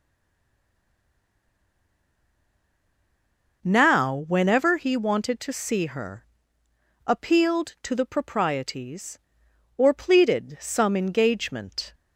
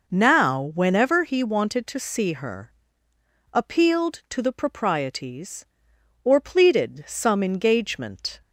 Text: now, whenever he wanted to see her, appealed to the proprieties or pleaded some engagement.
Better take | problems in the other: second | stays silent before the first word; strong; until 3.6 s; 3.6 s long

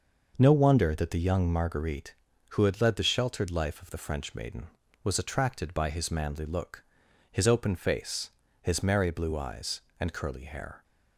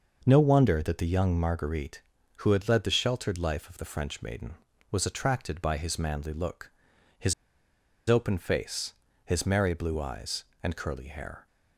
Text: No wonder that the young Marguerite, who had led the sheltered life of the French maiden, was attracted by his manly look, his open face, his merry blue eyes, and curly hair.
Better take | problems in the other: first | pauses between "his" and "open"; noticeable; at 7.3 s; 0.74 s long

